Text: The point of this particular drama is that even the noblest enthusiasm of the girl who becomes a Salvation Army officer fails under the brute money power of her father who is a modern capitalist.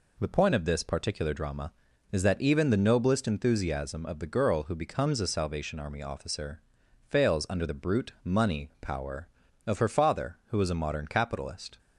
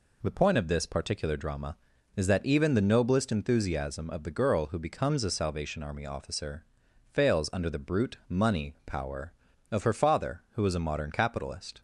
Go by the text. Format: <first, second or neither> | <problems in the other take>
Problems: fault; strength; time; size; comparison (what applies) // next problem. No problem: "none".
neither | pauses between "officer" and "fails"; noticeable; the same in both